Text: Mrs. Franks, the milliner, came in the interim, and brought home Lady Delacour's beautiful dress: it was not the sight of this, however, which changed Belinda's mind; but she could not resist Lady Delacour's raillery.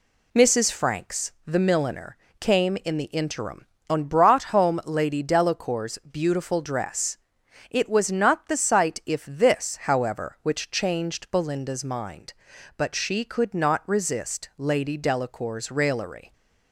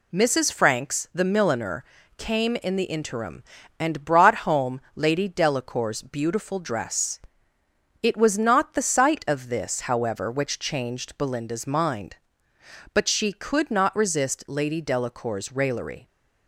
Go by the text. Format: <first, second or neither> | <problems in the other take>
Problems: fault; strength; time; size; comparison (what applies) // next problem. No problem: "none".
second | says "if" for "of"; at 9.0 s